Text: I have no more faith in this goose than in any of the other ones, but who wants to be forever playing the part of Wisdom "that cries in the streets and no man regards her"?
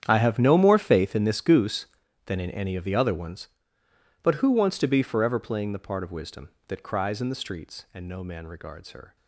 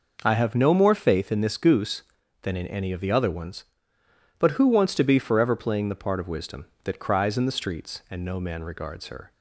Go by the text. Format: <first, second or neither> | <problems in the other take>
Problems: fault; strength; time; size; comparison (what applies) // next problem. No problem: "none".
second | gets quieter; strong; throughout; 17 dB